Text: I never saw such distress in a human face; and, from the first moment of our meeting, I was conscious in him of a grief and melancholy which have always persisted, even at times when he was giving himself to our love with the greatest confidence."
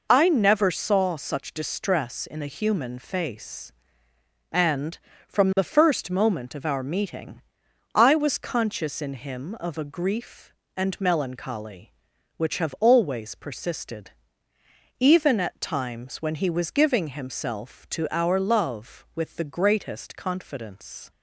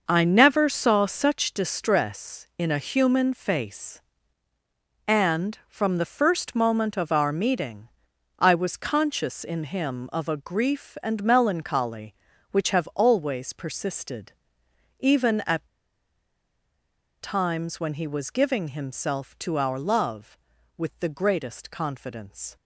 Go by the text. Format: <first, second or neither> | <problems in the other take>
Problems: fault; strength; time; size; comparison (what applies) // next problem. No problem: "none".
first | pauses between "at" and "times"; strong; at 15.6 s; 1.5 s long